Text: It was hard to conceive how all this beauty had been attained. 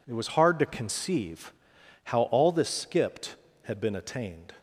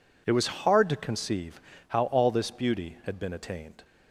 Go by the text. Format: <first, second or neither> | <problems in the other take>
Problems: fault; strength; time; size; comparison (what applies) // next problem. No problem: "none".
second | pauses between "conceive" and "how"; noticeable; at 1.5 s; 0.52 s long; slight in the second // says "skipped" for "beauty"; at 2.6 s